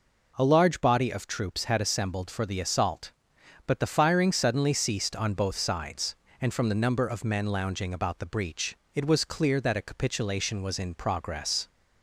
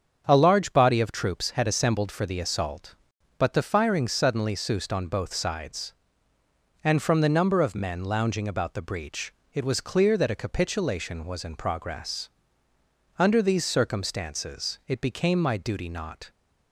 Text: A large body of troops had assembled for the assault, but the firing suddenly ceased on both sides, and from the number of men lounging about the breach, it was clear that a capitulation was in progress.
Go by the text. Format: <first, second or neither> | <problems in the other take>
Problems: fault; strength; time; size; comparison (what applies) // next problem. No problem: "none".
first | starts louder than the rest; strong; until 1.3 s; 7 dB // goes on to say "Under these circumstances it became my duty not"; strong; from 13.1 s on; 3.1 s long